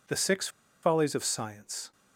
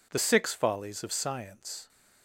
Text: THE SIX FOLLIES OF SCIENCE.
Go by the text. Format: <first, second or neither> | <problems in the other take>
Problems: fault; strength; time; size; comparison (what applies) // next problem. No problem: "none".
second | pauses between "SIX" and "FOLLIES"; slight; at 0.4 s; 0.34 s long